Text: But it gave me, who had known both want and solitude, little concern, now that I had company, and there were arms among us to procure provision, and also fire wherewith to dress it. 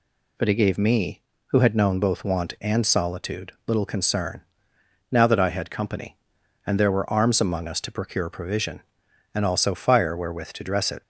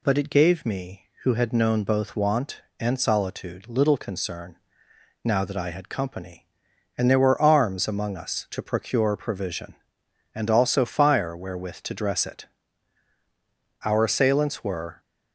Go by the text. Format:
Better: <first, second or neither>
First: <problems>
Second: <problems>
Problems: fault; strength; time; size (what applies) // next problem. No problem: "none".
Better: first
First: none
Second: goes on to say "Our assailants were"; noticeable; from 13.8 s on; 1.1 s long